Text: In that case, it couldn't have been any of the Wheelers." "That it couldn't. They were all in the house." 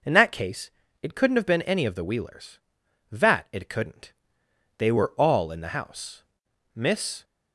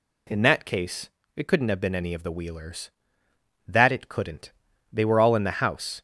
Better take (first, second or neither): second